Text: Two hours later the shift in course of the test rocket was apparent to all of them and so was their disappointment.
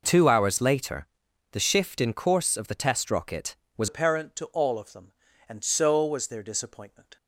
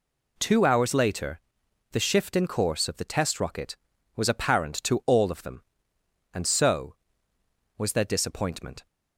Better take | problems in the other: second | pauses between "later" and "the"; noticeable; at 1.0 s; 0.46 s long; noticeable in the second // changes voice at "apparent"; from 3.8 s on; 3.3 s long

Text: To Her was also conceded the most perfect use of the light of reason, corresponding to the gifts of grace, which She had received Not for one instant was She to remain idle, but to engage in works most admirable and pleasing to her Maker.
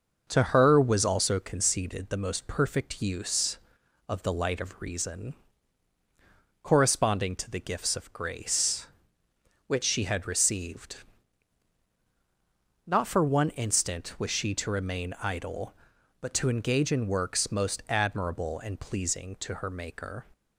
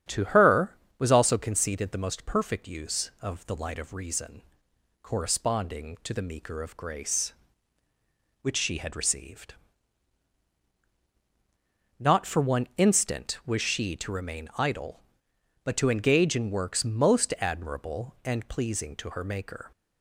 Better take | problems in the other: first | starts louder than the rest; strong; until 1.3 s; 9 dB // says "meeker" for "gifts"; at 6.2 s // pauses between "received" and "Not"; strong; at 9.5 s; 2.4 s long; strong in the first

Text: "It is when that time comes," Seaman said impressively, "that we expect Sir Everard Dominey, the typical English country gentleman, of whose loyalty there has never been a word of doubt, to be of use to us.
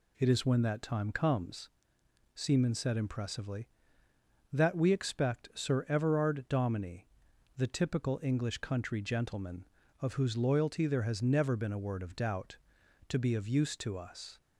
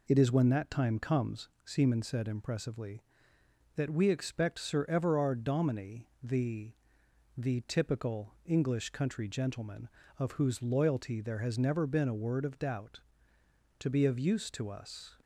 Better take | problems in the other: first | says "the" twice; at 7.3 s

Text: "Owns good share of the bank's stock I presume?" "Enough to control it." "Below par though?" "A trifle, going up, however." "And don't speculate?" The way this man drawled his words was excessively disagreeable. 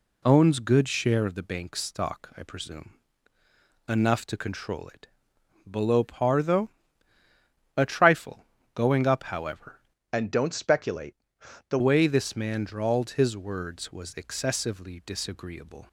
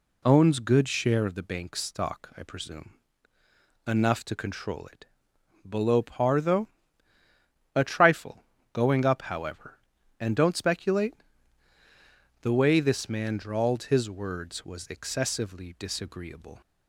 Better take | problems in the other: second | changes voice from "And" to "The"; from 10.1 to 11.7 s; 1.6 s long

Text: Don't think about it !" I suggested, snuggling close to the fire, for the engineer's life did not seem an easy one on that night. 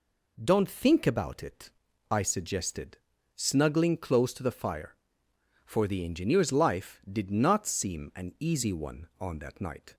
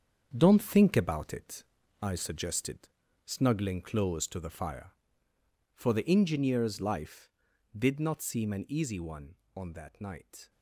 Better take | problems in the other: first | gets quieter; throughout; 6.5 dB

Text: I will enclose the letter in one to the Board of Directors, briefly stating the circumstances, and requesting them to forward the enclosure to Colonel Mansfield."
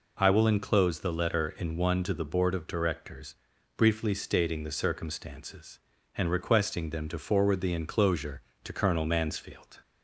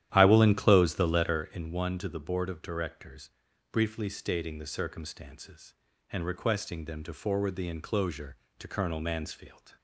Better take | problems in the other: first | starts louder than the rest; strong; until 1.5 s; 11.5 dB

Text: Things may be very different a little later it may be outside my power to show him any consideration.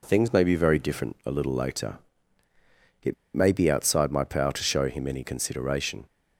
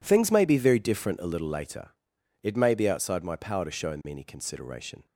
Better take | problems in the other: second | pauses between "later" and "it"; at 1.9 s; 1.0 s long; noticeable in the second // pauses between "it" and "may"; slight; at 3.1 s; 0.21 s long

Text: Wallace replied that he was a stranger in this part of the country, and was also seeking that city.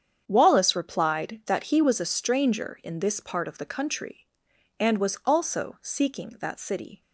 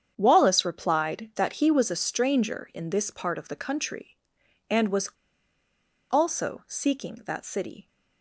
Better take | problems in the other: first | starts louder than the rest; strong; until 1.1 s; 8 dB; strong in the first // pauses between "was" and "also"; at 5.0 s; 1.0 s long

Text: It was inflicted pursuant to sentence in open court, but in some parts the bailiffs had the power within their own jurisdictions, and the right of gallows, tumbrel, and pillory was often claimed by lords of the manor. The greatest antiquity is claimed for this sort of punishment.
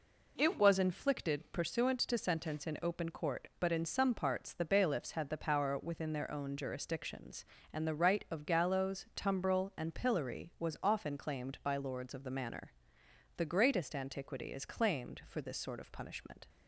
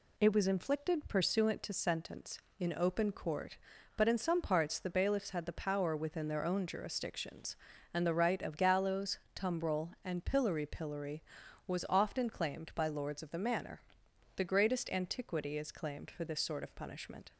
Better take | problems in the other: first | says "pillory" twice; at 10.6 s

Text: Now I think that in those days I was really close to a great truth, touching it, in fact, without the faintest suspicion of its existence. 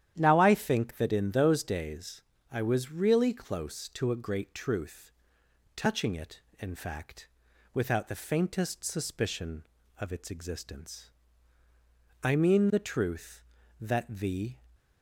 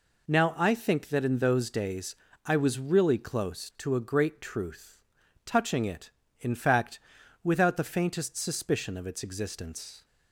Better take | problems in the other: second | starts louder than the rest; strong; until 1.1 s; 10.5 dB // pauses between "days" and "I"; slight; at 2.2 s; 0.28 s long; slight in the second // goes on to say "I mean the truth that the"; strong; from 12.2 s on; 2.3 s long

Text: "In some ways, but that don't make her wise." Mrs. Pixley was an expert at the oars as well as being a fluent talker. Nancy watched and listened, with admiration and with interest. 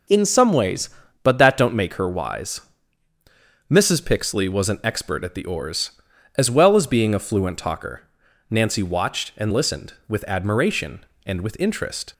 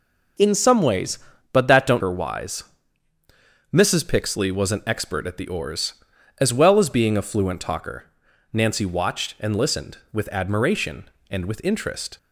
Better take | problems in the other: first | skips "make"; at 2.0 s

